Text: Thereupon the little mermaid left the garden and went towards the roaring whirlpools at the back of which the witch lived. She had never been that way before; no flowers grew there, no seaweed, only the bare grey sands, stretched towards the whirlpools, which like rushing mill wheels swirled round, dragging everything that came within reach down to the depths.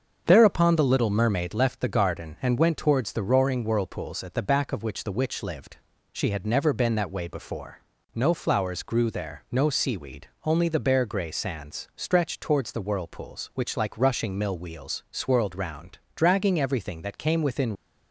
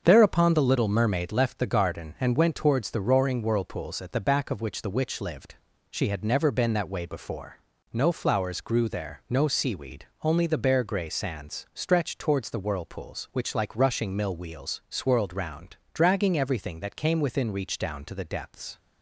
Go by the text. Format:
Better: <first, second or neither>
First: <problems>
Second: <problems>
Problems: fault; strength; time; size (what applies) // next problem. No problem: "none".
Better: second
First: starts louder than the rest; until 1.2 s; 6.5 dB // stops before "reach down to the depths"; at 17.7 s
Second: starts louder than the rest; until 1.0 s; 6.5 dB